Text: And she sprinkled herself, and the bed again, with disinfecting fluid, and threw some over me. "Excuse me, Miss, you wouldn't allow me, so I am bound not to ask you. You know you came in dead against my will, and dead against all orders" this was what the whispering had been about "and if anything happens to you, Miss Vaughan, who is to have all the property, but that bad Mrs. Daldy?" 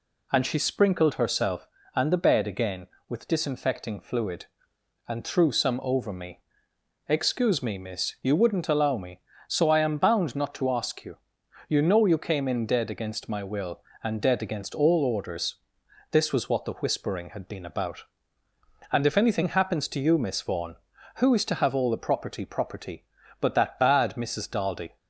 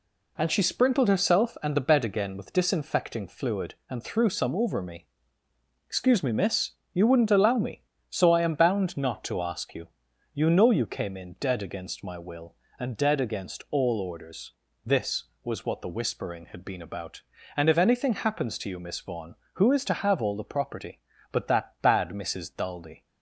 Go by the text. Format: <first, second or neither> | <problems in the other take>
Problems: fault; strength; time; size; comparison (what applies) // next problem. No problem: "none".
second | pauses between "orders" and "this"; noticeable; at 15.5 s; 0.58 s long; slight in the second // says "property" twice; at 22.4 s